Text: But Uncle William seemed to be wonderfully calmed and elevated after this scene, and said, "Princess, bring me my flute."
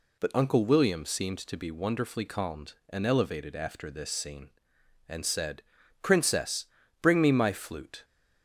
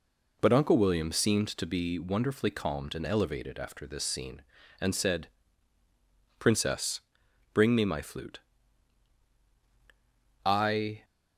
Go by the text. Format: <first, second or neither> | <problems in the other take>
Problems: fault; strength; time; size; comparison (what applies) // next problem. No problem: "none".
first | goes on to say "I"; from 10.4 s on; 0.60 s long